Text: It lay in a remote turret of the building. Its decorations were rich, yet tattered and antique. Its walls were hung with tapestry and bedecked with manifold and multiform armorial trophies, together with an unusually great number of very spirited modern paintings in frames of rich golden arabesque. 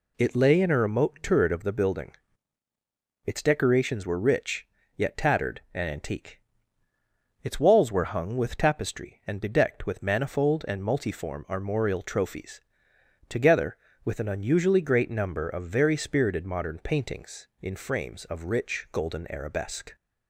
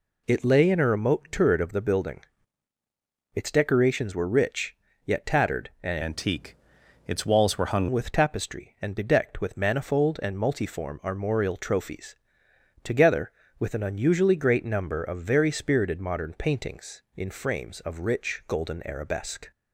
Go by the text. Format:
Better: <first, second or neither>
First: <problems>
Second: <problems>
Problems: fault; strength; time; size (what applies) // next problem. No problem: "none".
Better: first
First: none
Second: changes voice from "antique" to "hung"; from 6.0 to 7.8 s; 1.8 s long